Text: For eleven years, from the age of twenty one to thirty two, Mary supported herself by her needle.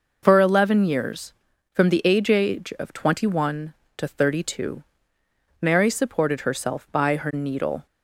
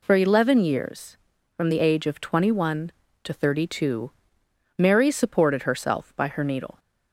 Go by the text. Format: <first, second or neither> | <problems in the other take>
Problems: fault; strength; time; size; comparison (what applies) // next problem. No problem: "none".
second | says "age" twice; at 2.2 s